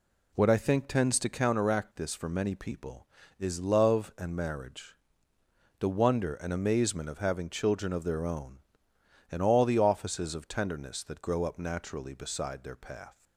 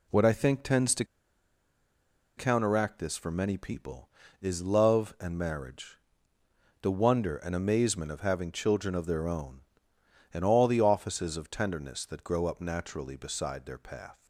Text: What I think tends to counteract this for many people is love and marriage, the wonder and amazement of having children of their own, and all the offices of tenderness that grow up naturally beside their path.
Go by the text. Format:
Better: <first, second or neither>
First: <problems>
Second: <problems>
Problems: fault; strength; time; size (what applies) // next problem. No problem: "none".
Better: first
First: none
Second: pauses between "to" and "counteract"; strong; at 1.0 s; 1.3 s long